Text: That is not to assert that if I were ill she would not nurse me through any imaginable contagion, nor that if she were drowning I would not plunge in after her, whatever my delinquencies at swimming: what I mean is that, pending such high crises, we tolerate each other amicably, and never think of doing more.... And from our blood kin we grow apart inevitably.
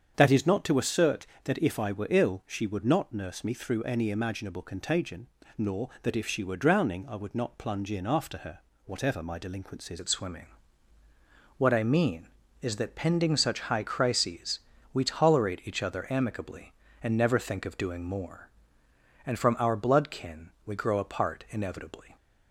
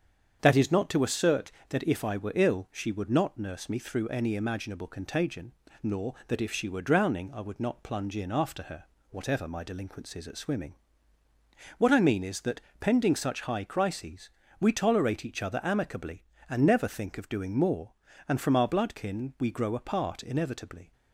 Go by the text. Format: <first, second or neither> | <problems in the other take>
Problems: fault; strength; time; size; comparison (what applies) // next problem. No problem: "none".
second | starts louder than the rest; strong; until 1.1 s; 7.5 dB; strong in the second // changes voice at "at"; from 9.9 s on; 12.2 s long